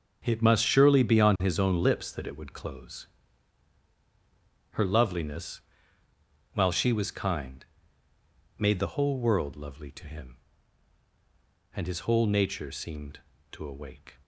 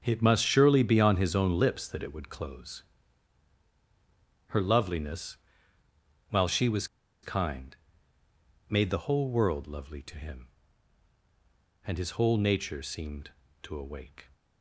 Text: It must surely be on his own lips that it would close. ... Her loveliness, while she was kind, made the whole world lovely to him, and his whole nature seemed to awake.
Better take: first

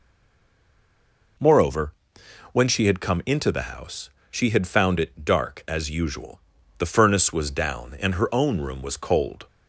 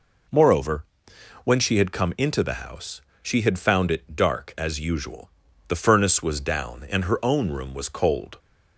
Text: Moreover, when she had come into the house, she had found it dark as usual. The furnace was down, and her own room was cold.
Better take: second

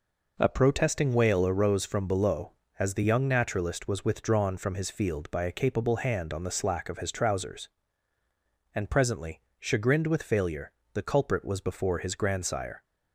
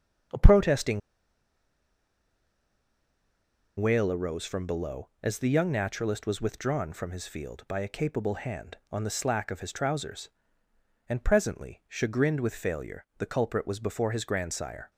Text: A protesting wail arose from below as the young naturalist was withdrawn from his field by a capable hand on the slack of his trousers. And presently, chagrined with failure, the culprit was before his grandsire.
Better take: first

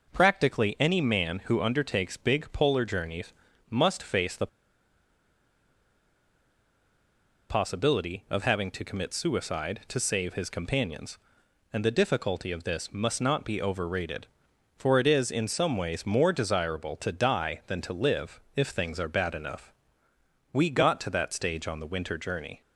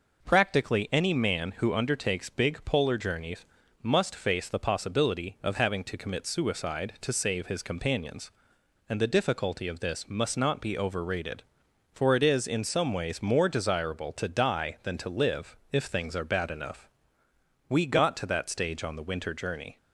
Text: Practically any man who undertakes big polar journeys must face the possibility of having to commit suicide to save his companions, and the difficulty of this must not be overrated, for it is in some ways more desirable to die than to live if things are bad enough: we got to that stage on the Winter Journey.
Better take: second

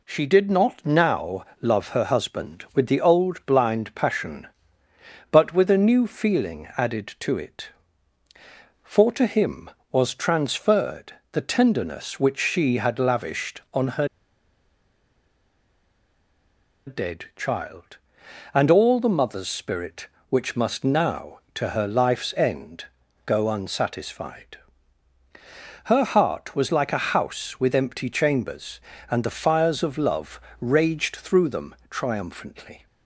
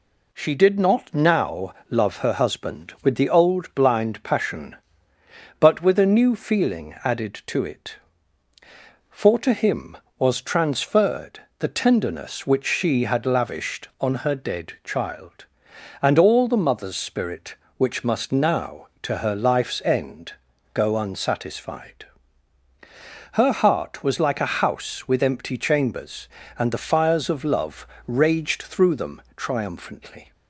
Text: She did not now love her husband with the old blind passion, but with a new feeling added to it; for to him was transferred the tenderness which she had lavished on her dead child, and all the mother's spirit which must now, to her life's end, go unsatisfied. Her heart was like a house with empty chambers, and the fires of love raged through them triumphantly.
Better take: second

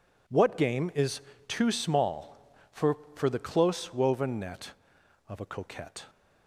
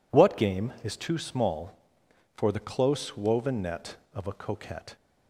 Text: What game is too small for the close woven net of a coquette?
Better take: second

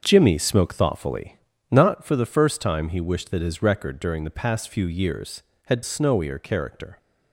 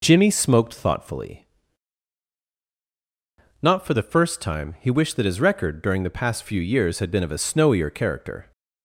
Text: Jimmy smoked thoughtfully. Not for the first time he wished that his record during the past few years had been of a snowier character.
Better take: second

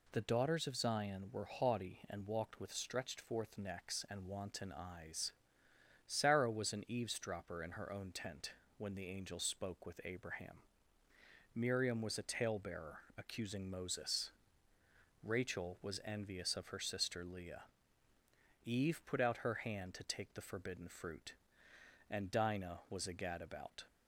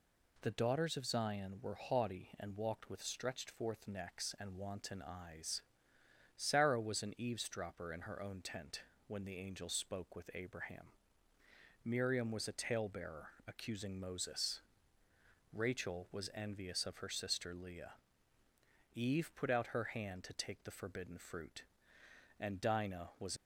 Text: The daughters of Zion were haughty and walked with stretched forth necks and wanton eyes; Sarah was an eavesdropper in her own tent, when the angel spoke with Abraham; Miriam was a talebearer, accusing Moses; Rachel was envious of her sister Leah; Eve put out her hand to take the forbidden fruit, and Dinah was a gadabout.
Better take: first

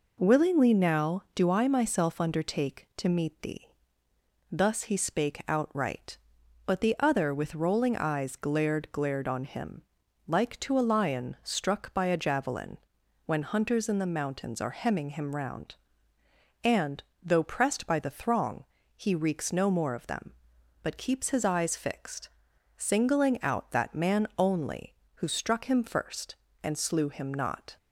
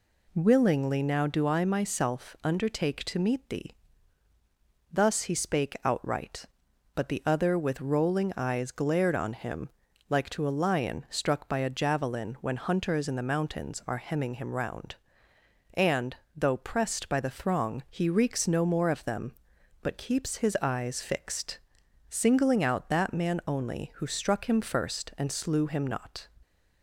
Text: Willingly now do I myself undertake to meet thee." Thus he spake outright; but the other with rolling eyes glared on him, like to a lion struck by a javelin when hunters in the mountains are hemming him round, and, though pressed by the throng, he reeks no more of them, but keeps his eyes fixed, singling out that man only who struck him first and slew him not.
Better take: second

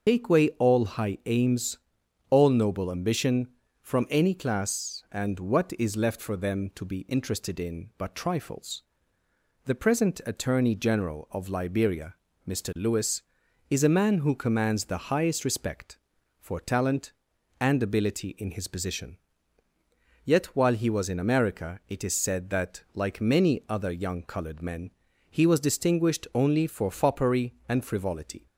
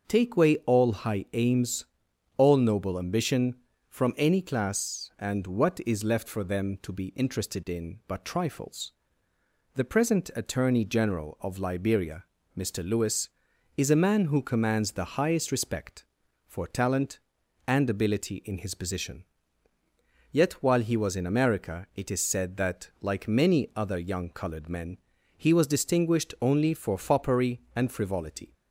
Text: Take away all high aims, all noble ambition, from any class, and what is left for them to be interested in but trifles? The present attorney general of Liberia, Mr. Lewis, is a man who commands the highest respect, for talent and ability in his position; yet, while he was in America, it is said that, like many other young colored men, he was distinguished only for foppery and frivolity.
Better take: second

